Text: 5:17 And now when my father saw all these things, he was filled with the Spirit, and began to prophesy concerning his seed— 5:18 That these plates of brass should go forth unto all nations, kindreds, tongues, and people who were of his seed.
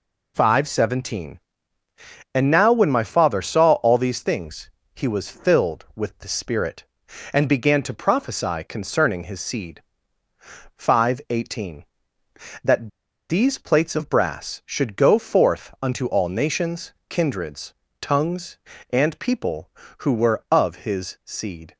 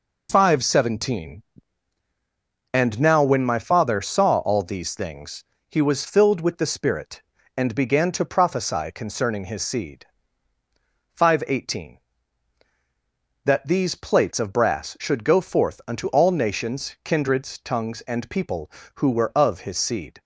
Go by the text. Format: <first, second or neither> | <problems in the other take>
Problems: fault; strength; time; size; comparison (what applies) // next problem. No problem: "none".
second | pauses between "That" and "these"; at 12.8 s; 0.40 s long